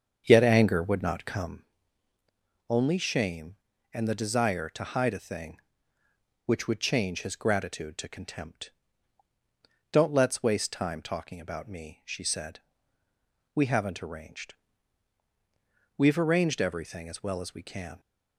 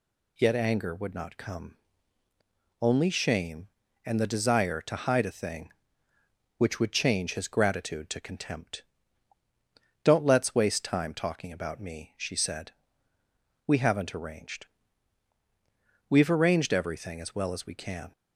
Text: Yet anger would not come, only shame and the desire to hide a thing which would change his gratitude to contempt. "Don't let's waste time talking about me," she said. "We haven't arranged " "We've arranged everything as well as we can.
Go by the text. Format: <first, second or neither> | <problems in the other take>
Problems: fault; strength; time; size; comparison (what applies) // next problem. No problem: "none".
second | starts louder than the rest; until 1.7 s; 7 dB